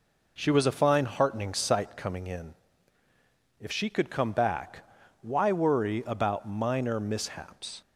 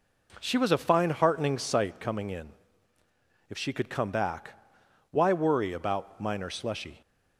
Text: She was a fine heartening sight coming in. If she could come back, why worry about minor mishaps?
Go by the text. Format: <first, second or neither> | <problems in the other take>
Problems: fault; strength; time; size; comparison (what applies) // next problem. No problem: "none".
first | says "slushy" for "mishaps"; at 6.4 s